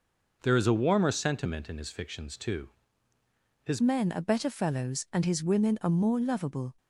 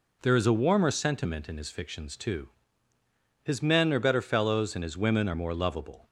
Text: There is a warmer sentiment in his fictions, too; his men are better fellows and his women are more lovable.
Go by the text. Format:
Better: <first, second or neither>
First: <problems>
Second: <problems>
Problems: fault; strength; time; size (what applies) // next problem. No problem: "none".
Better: second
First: changes voice at "men"; from 3.7 s on; 3.0 s long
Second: none